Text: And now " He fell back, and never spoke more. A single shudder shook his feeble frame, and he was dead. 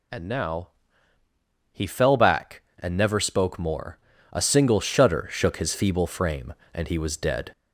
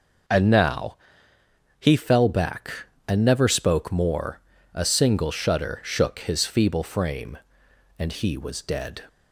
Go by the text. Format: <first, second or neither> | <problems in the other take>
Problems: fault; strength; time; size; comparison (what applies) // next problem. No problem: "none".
second | gets louder; strong; throughout; 15.5 dB